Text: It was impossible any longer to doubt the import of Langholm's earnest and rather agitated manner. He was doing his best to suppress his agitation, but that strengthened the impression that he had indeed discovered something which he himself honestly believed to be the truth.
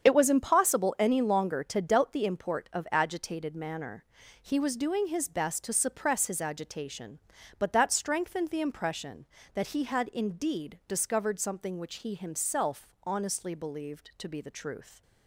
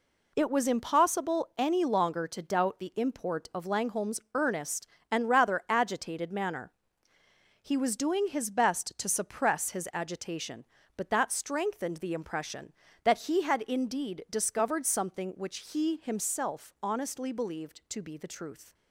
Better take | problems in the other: second | starts louder than the rest; strong; until 1.0 s; 7.5 dB // skips "Langholm's earnest and rather"; at 2.8 s // pauses between "himself" and "honestly"; slight; at 12.8 s; 0.16 s long

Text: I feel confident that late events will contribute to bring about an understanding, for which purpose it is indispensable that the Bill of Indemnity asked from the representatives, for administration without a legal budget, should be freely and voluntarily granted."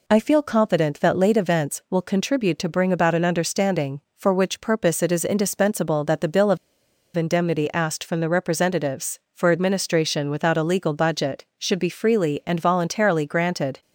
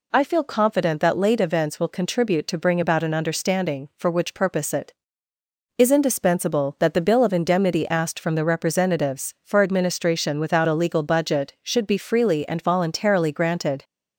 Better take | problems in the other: second | pauses between "of" and "Indemnity"; noticeable; at 6.5 s; 0.59 s long

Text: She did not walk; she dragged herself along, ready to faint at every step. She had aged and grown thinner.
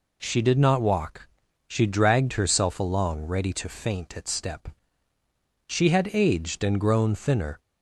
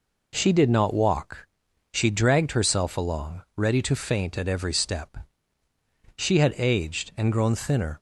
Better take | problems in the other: second | skips "every"; at 4.2 s

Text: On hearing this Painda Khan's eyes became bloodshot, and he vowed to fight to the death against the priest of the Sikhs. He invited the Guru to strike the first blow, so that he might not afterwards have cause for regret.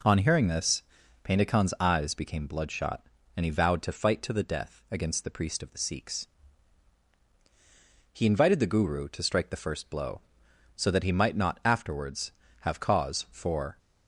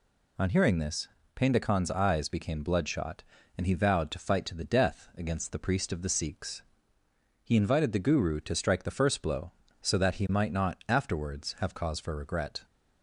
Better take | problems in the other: second | pauses between "this" and "Painda"; at 0.8 s; 0.42 s long; slight in the second // stops before "regret"; at 13.7 s

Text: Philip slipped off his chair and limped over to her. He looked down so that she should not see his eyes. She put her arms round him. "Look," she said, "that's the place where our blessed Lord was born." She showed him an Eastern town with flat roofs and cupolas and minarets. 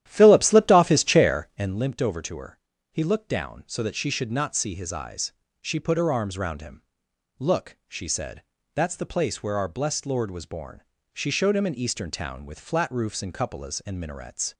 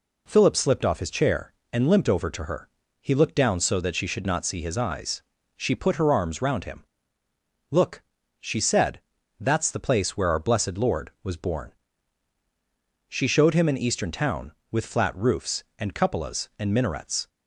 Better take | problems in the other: second | starts louder than the rest; strong; until 1.8 s; 11.5 dB

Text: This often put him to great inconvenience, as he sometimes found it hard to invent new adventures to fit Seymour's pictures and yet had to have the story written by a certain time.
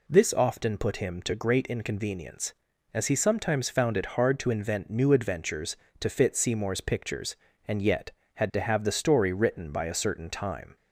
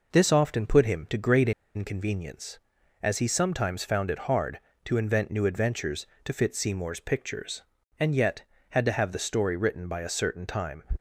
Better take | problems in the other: first | pauses between "great" and "inconvenience"; slight; at 1.5 s; 0.25 s long

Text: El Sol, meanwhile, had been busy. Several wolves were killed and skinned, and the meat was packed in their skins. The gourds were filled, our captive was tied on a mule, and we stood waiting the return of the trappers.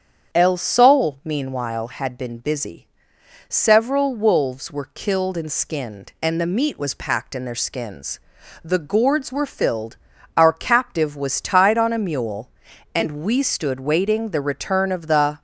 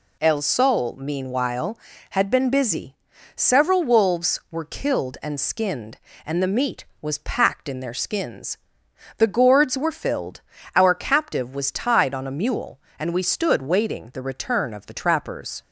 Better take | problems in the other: second | starts louder than the rest; strong; until 1.4 s; 8 dB // stops before "trappers"; at 15.3 s

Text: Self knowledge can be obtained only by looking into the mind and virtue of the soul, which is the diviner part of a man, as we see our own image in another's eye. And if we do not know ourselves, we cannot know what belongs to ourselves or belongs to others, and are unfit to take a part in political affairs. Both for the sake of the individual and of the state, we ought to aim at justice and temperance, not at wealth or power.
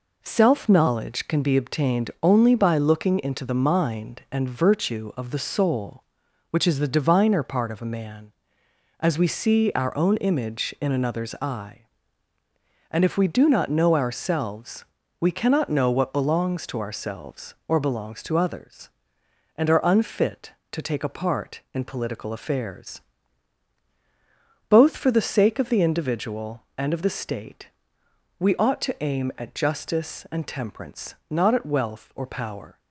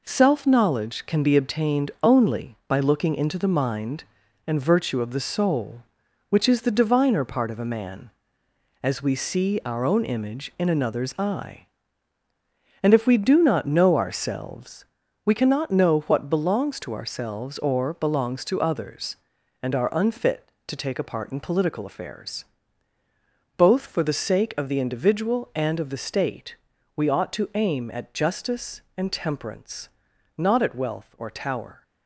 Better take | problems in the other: first | says "tower" for "power"; at 31.3 s

